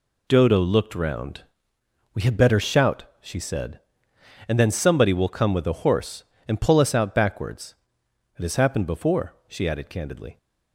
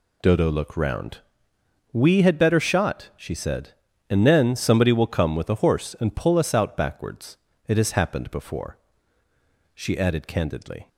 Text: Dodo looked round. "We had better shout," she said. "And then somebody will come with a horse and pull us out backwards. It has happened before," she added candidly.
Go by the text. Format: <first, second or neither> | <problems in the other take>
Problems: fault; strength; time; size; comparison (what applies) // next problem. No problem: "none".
first | says "shot" for "shout"; at 2.5 s